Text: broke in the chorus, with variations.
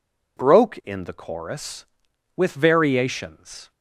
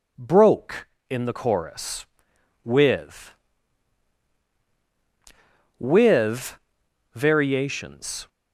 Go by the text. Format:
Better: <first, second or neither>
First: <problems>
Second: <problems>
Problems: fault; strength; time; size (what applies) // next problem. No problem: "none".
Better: first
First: none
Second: says "with" twice; at 5.7 s